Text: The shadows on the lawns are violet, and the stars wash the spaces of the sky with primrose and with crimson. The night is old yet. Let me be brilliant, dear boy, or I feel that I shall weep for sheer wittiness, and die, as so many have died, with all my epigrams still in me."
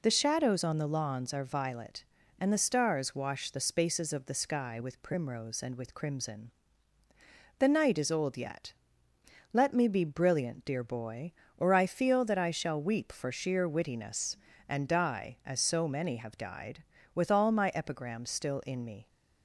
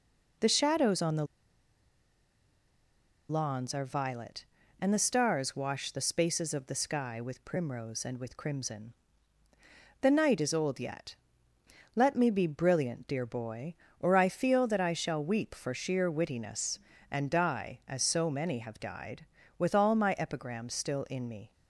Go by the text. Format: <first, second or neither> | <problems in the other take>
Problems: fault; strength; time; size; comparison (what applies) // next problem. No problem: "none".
first | pauses between "the" and "lawns"; strong; at 1.2 s; 2.0 s long